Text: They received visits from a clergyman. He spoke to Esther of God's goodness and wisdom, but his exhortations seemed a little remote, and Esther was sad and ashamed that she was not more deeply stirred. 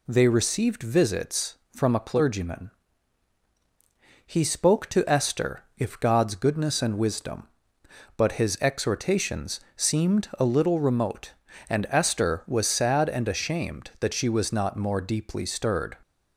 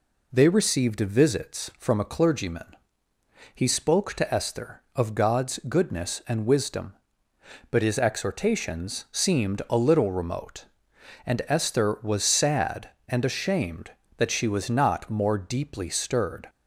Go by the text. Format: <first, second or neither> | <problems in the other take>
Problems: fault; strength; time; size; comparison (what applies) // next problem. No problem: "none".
second | says "if" for "of"; at 5.7 s // pauses between "exhortations" and "seemed"; slight; at 9.5 s; 0.16 s long